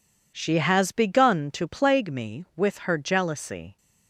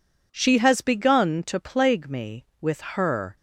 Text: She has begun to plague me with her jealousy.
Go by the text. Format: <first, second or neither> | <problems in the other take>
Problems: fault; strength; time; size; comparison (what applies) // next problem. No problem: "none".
first | stops before "jealousy"; at 3.3 s